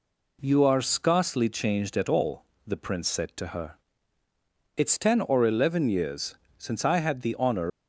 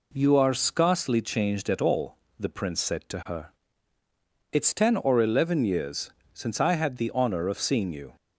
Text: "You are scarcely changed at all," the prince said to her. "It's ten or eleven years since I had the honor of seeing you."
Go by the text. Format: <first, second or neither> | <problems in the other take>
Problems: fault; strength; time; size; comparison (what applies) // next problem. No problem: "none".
second | pauses between "years" and "since"; slight; at 6.3 s; 0.22 s long; slight in the second // stops before "of seeing you"; at 7.7 s